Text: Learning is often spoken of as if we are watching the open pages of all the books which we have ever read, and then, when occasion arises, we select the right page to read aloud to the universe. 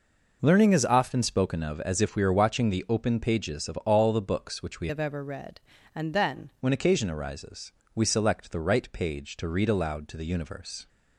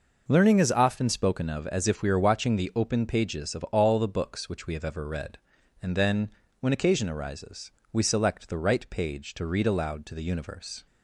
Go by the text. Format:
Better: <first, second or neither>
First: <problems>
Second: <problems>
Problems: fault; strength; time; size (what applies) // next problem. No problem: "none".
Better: second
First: changes voice from "have" to "then"; from 4.8 to 6.4 s; 1.6 s long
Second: none